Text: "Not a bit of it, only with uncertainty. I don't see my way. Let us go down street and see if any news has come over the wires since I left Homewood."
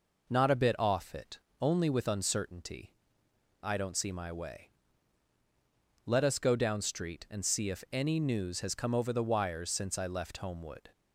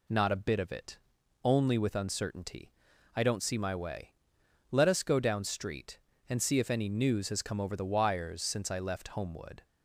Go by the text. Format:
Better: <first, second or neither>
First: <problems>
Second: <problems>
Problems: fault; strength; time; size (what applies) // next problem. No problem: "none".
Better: second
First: says "off" for "of"; at 0.7 s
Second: none